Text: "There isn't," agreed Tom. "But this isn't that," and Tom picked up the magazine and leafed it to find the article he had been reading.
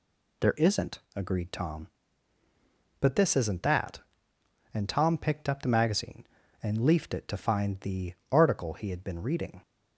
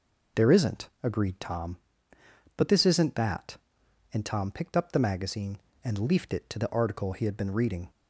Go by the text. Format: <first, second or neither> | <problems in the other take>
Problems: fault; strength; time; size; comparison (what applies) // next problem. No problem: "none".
first | skips "find"; at 6.5 s